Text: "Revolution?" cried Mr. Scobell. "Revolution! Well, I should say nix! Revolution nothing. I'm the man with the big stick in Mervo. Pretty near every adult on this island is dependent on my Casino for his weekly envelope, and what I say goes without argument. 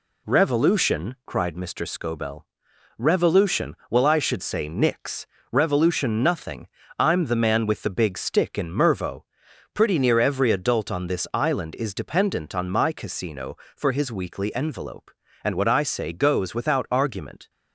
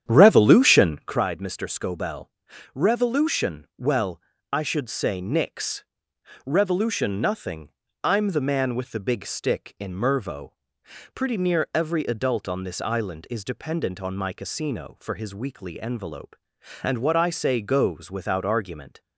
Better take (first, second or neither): first